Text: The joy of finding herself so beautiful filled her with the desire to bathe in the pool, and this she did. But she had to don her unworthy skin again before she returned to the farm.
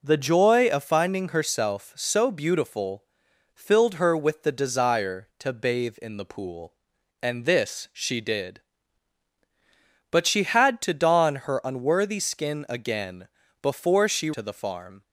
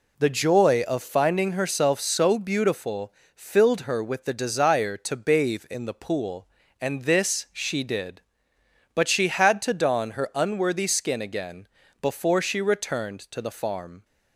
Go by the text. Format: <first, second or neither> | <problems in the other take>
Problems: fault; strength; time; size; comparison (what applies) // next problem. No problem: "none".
second | pauses between "beautiful" and "filled"; noticeable; at 3.0 s; 0.50 s long; slight in the second // pauses between "again" and "before"; slight; at 13.2 s; 0.34 s long; slight in the second // skips "returned"; at 14.3 s